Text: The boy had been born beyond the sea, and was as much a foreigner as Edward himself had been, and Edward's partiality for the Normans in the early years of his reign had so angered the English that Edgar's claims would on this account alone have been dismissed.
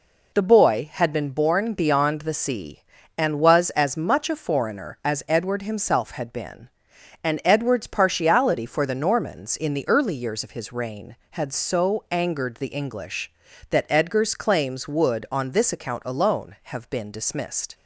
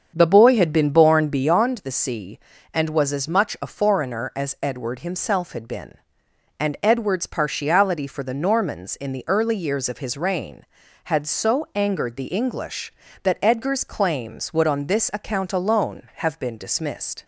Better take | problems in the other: first | starts louder than the rest; strong; until 1.5 s; 7 dB

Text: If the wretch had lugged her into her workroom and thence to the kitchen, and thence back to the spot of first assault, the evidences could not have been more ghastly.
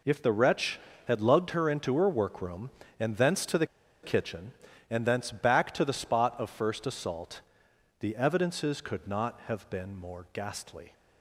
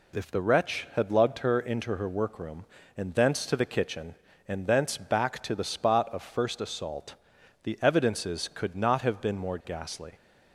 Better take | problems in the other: second | pauses between "the" and "kitchen"; at 3.6 s; 0.36 s long

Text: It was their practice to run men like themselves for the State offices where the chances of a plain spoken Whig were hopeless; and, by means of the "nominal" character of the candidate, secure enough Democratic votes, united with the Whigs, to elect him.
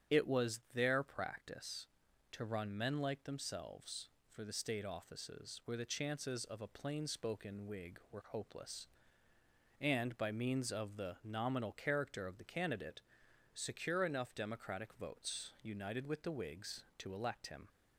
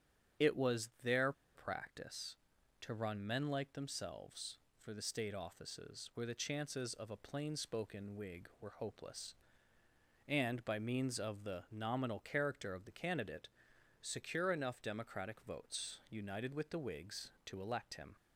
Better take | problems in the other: first | starts louder than the rest; strong; until 1.7 s; 8.5 dB; strong in the first // pauses between "their" and "practice"; slight; at 1.3 s; 0.23 s long

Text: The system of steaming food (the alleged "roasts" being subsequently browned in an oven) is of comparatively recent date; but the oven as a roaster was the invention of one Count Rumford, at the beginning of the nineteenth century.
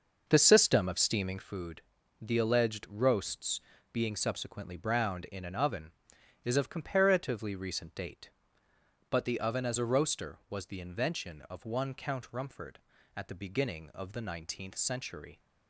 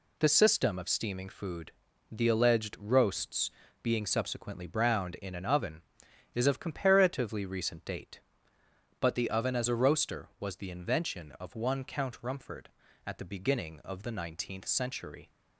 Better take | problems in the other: second | starts louder than the rest; noticeable; until 1.5 s; 6 dB // pauses between "roasts" and "being"; slight; at 3.6 s; 0.32 s long; slight in the second

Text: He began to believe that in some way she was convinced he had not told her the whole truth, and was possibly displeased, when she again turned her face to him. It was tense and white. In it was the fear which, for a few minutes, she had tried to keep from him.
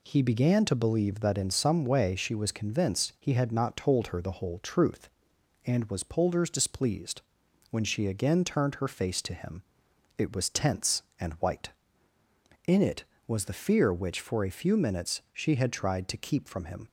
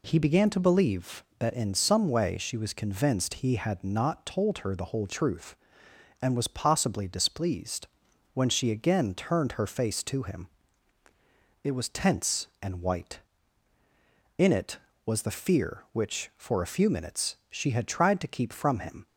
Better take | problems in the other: second | says "polders" for "possibly"; at 6.0 s

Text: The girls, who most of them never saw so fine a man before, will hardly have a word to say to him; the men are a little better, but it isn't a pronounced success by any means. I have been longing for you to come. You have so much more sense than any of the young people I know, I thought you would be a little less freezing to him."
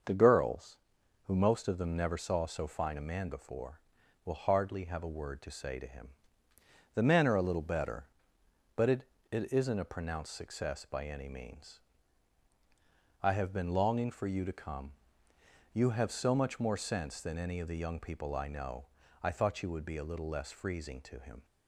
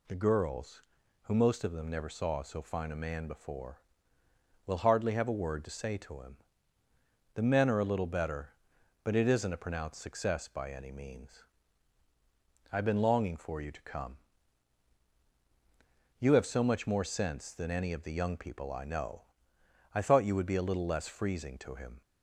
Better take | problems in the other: second | starts louder than the rest; until 1.5 s; 6.5 dB // says "it" twice; at 9.3 s

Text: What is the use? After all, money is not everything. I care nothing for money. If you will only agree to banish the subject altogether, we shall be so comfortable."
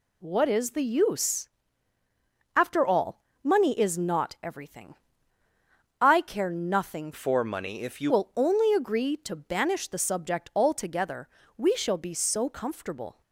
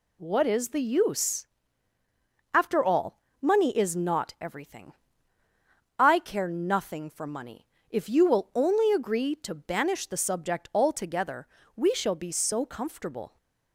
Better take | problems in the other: second | changes voice from "for" to "you"; from 7.1 to 8.1 s; 1.0 s long

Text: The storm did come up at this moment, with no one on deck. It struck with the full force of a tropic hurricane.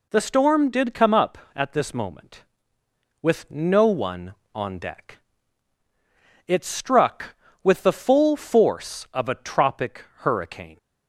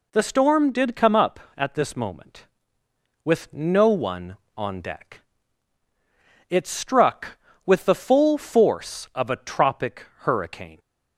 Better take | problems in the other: neither | none

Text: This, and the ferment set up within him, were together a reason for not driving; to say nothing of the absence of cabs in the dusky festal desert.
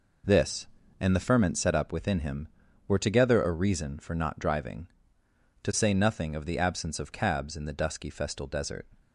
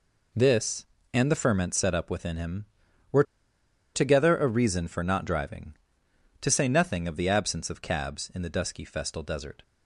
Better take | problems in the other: first | pauses between "were" and "together"; noticeable; at 3.2 s; 0.72 s long

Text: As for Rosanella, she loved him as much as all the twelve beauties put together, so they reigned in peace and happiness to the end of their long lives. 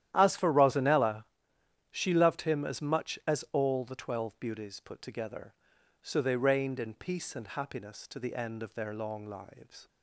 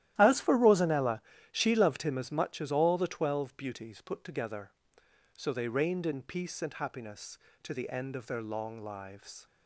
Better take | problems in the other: neither | starts louder than the rest; strong; the same in both

